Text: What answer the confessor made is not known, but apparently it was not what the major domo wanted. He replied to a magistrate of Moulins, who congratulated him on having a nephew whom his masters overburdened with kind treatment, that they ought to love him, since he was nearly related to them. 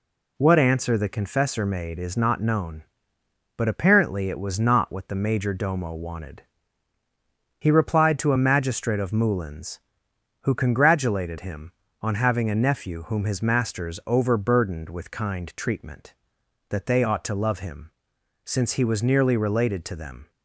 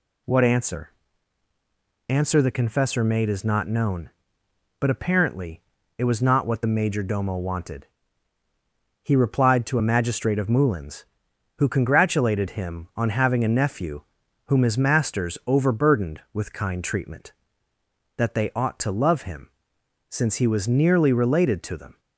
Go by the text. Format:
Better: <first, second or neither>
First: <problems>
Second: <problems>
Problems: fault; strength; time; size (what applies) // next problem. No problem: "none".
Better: first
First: none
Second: says "answer" twice; at 2.0 s // pauses between "apparently" and "it"; slight; at 5.6 s; 0.36 s long // pauses between "nephew" and "whom"; at 14.0 s; 0.44 s long